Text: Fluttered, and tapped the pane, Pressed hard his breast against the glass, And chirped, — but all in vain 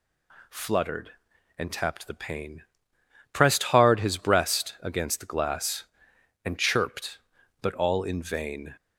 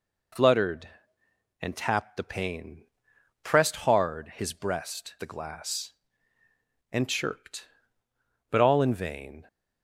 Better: first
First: none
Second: skips "against"; at 5.1 s

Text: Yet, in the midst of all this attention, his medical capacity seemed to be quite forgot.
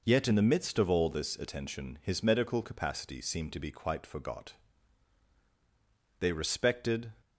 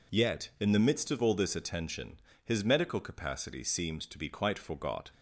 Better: second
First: goes on to say "They respected"; noticeable; from 6.1 s on; 0.94 s long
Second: none

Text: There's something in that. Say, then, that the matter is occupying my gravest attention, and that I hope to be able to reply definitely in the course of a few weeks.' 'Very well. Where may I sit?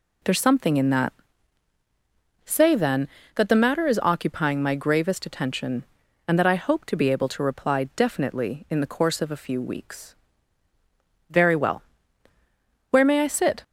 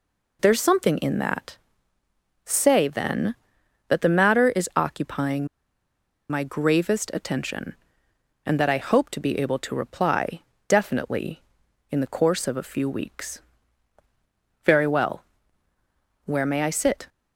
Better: first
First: none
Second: pauses between "occupying" and "my"; noticeable; at 5.4 s; 0.83 s long // pauses between "reply" and "definitely"; slight; at 10.4 s; 0.26 s long

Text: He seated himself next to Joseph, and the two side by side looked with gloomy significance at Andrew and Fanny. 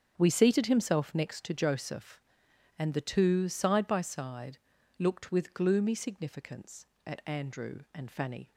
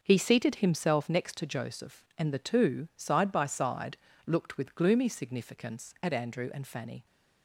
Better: second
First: starts louder than the rest; strong; until 1.1 s; 7.5 dB // says "We" for "He"; at 0.1 s // pauses between "side" and "looked"; at 4.5 s; 0.42 s long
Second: starts louder than the rest; until 1.0 s; 6.5 dB // pauses between "side" and "looked"; slight; at 3.9 s; 0.28 s long

